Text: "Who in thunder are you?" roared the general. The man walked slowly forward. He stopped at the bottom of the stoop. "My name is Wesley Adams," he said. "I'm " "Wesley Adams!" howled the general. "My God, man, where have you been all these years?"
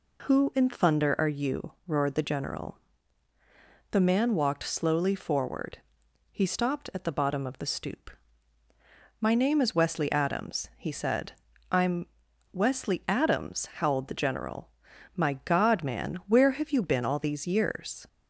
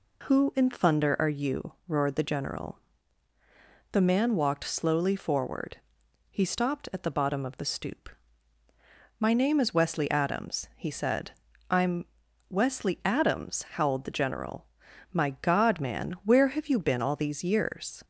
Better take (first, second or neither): neither